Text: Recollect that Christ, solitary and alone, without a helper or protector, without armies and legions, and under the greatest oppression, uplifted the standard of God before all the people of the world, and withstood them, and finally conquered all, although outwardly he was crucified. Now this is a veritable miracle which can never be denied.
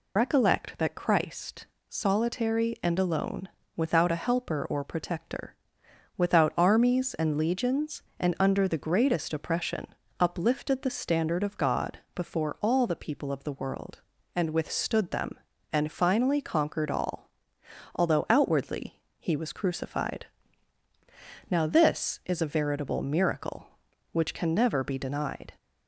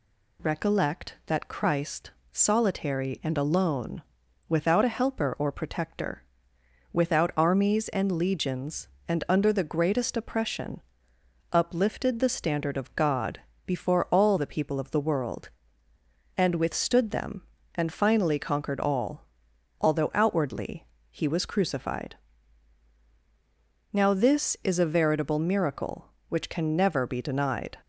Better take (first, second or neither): second